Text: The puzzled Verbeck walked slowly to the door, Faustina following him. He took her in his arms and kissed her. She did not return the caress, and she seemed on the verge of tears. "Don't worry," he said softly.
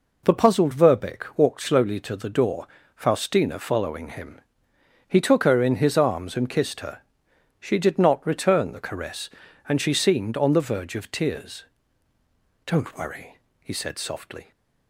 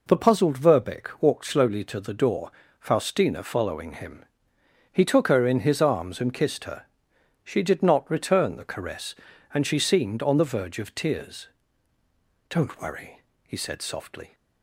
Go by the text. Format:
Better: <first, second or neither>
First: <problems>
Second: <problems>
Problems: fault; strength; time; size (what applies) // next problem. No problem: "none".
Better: neither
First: none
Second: none